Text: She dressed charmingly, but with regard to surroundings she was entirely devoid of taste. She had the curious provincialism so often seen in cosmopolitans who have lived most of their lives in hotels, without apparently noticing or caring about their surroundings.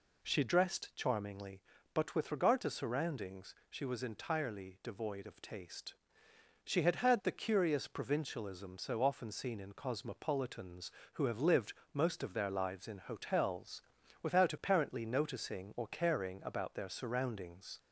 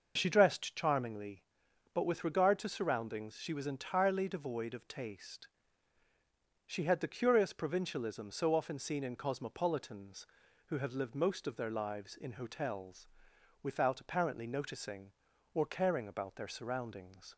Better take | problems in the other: second | says "had" twice; at 6.9 s // pauses between "lived" and "most"; slight; at 11.7 s; 0.20 s long

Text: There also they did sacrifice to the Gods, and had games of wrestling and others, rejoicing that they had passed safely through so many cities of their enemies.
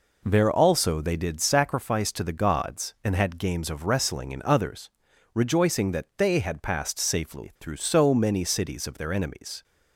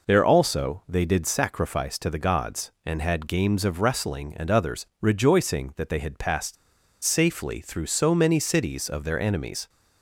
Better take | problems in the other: first | pauses between "passed" and "safely"; noticeable; at 6.5 s; 0.49 s long

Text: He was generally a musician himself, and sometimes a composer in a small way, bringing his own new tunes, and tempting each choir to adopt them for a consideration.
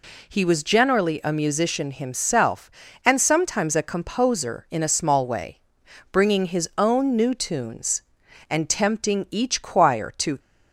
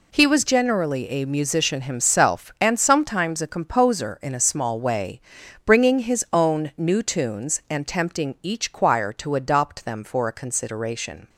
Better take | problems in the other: second | stops before "adopt them for a consideration"; at 10.3 s

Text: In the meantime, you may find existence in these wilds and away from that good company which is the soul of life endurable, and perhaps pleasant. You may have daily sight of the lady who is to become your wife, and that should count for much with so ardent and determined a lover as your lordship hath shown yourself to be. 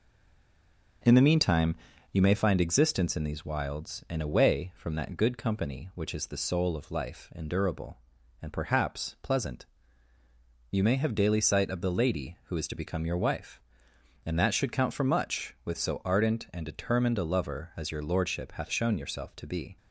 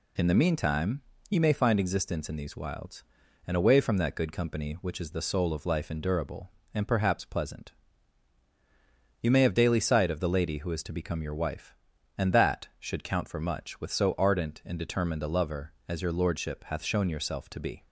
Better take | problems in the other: second | stays silent before the first word; until 1.0 s; 1.0 s long

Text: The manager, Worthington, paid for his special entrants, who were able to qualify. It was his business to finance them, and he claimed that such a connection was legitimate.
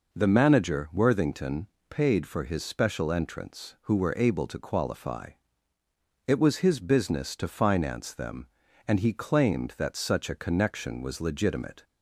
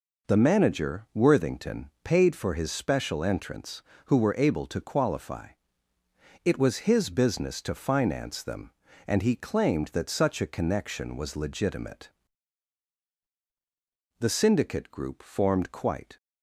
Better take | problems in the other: first | goes on to say "The Syndicate group formed quite"; strong; from 14.2 s on; 1.9 s long

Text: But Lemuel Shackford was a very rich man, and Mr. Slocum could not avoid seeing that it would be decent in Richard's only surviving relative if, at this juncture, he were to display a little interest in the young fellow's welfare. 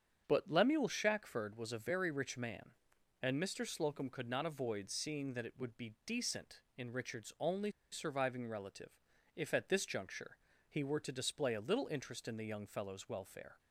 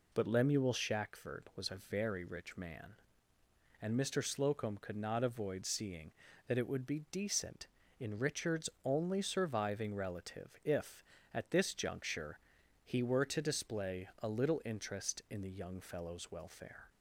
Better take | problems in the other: second | starts louder than the rest; strong; until 1.2 s; 7.5 dB // pauses between "only" and "surviving"; slight; at 7.7 s; 0.21 s long // pauses between "relative" and "if"; slight; at 8.9 s; 0.36 s long

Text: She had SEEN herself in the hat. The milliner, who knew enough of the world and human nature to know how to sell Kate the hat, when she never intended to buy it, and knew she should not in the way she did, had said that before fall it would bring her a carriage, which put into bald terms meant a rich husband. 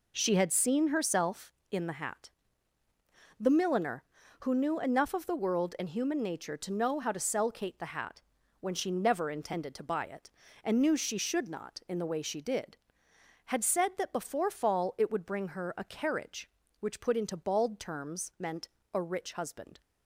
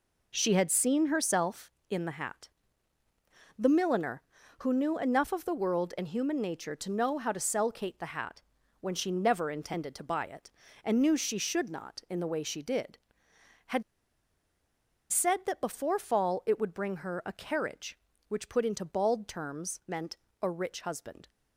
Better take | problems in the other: first | pauses between "had" and "said"; strong; at 13.8 s; 1.3 s long // pauses between "meant" and "a"; slight; at 20.1 s; 0.24 s long; slight in the first

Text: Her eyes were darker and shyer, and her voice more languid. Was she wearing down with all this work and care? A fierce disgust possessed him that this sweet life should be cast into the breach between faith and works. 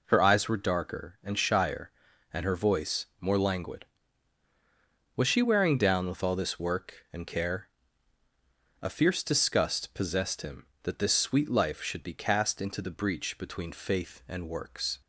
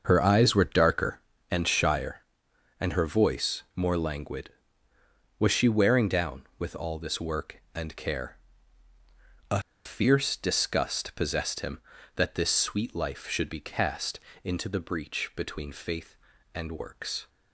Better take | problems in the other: first | starts louder than the rest; until 1.0 s; 6.5 dB // pauses between "A" and "fierce"; slight; at 9.5 s; 0.25 s long // pauses between "cast" and "into"; slight; at 14.1 s; 0.24 s long

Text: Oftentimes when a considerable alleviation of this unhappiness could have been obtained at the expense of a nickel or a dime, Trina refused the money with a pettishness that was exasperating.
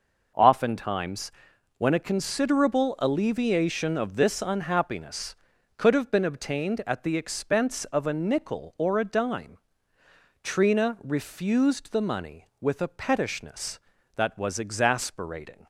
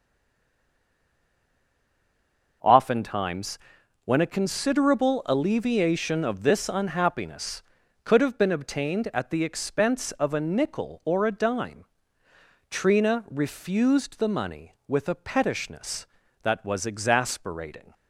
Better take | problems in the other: first | stays silent before the first word; strong; until 2.6 s; 2.6 s long // pauses between "Oftentimes" and "when"; noticeable; at 3.5 s; 0.48 s long; noticeable in the first

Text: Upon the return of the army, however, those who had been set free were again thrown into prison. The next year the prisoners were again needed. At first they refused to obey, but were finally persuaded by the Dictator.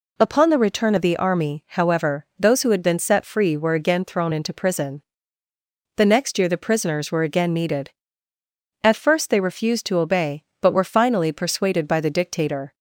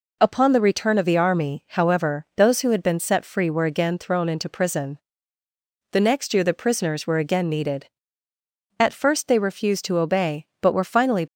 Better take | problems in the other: first | stops before "persuaded by the Dictator"; at 11.2 s

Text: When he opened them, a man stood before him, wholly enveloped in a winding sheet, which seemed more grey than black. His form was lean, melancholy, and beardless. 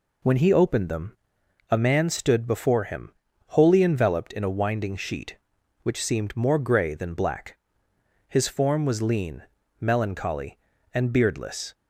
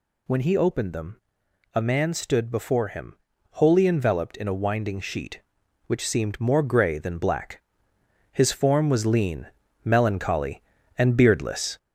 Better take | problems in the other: first | gets louder; noticeable; throughout; 4.5 dB

